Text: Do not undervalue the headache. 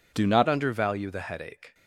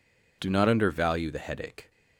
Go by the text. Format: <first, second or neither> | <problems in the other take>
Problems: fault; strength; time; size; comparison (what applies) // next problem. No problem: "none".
second | changes voice at "undervalue"; from 0.4 s on; 1.3 s long